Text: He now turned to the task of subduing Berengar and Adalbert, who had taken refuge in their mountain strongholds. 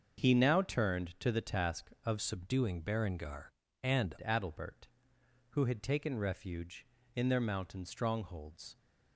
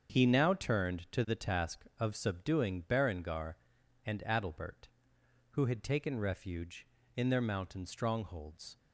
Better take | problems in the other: second | starts louder than the rest; until 1.2 s; 6.5 dB; also in the second // changes voice from "subduing" to "and"; from 2.2 to 4.1 s; 1.9 s long

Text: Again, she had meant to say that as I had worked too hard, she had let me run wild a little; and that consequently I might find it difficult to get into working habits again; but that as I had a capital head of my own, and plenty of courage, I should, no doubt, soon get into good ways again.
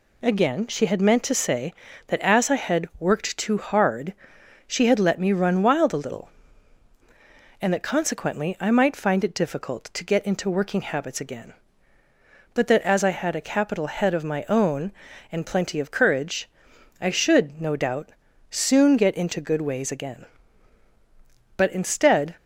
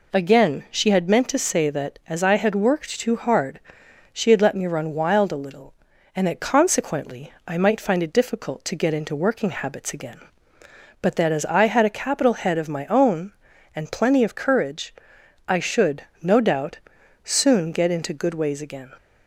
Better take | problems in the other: second | goes on to say "But instead"; noticeable; from 21.5 s on; 0.78 s long

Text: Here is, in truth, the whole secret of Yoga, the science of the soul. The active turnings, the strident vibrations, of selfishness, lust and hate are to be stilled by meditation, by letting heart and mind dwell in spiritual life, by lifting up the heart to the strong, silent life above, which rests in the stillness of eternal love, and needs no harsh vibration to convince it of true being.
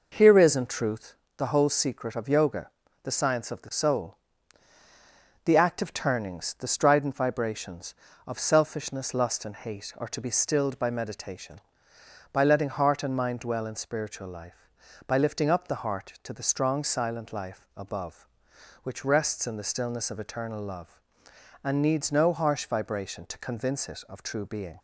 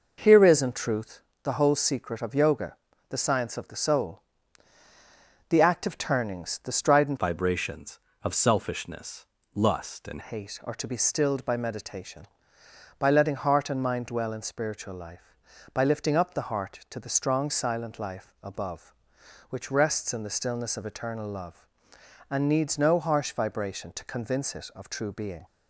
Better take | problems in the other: first | changes voice from "vibrations" to "and"; from 7.1 to 10.2 s; 3.1 s long

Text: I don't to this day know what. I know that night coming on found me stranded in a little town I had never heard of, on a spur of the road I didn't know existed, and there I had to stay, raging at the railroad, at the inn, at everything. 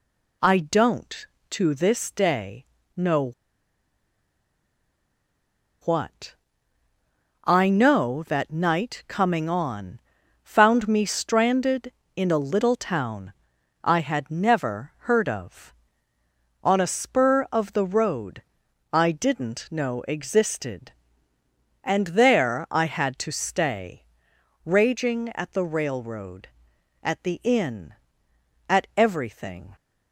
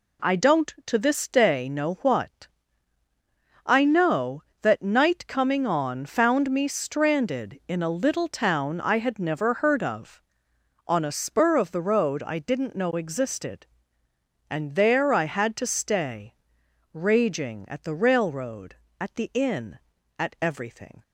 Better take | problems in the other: second | pauses between "day" and "know"; slight; at 2.6 s; 0.32 s long // pauses between "know" and "what"; strong; at 3.3 s; 2.5 s long // pauses between "on" and "found"; at 9.9 s; 0.44 s long // pauses between "town" and "I"; noticeable; at 13.3 s; 0.50 s long // pauses between "road" and "I"; noticeable; at 18.4 s; 0.50 s long

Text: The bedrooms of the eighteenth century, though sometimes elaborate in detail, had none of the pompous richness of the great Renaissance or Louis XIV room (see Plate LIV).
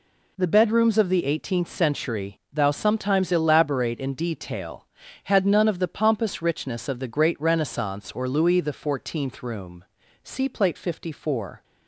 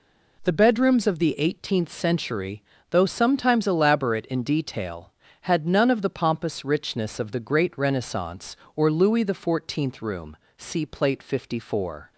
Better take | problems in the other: second | says "thou" for "though"; at 2.5 s

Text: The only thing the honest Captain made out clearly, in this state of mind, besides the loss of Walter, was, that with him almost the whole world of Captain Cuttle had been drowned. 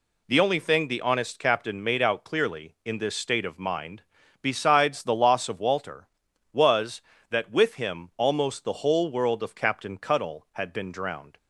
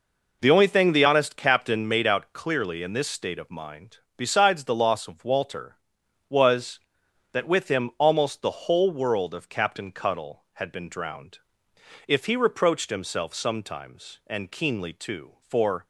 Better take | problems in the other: first | goes on to say "If he reproached himself sometimes and keenly too for"; strong; from 12.0 s on; 3.7 s long

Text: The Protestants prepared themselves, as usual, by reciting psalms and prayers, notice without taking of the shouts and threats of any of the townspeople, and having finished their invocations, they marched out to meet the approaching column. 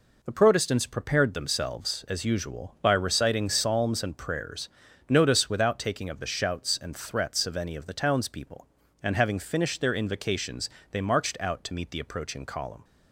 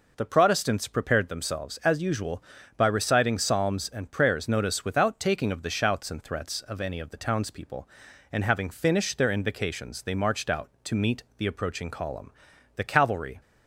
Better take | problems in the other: first | goes on to say "The cavalry"; noticeable; from 12.7 s on; 0.64 s long

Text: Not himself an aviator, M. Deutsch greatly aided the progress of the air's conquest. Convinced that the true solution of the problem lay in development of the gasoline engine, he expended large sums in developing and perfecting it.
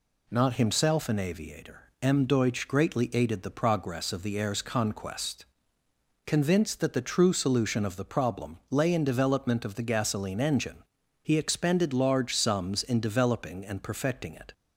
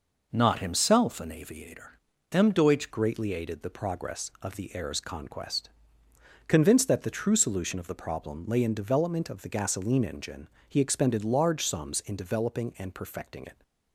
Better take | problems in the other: first | changes voice at "greatly"; from 2.9 s on; 10.7 s long

